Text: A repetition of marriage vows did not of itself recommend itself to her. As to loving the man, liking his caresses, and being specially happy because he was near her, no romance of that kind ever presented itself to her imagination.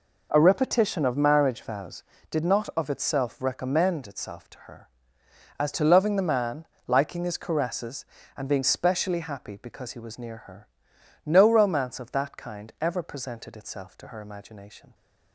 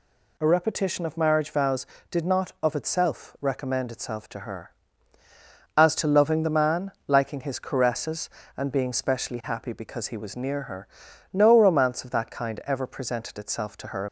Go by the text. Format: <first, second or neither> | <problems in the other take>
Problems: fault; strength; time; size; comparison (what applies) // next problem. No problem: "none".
first | stops before "imagination"; at 14.0 s